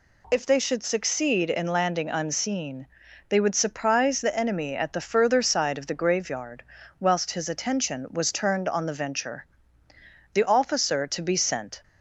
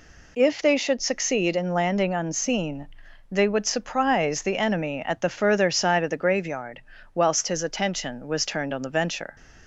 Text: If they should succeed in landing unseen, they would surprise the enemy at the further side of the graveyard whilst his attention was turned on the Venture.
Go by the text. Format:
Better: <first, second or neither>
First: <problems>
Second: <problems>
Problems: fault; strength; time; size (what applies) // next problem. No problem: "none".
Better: second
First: pauses between "graveyard" and "whilst"; at 6.6 s; 0.38 s long // goes on to say "The officer to be sent"; from 10.3 s on; 1.4 s long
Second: pauses between "graveyard" and "whilst"; slight; at 6.7 s; 0.36 s long